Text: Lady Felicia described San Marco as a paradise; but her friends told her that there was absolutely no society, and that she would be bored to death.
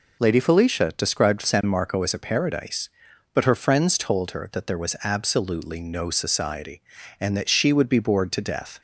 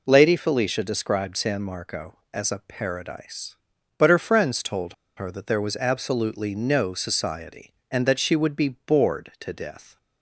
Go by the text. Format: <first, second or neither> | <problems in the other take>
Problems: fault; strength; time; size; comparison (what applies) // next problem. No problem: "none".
first | pauses between "told" and "her"; slight; at 4.9 s; 0.23 s long